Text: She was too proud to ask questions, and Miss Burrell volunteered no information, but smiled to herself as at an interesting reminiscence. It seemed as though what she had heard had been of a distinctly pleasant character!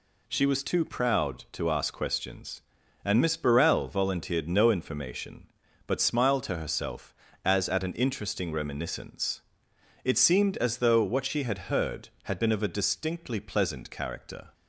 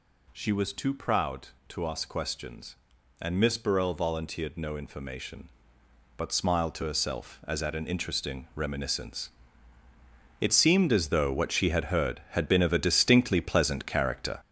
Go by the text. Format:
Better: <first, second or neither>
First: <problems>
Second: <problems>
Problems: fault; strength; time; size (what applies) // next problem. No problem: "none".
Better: first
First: none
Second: gets louder; throughout; 7 dB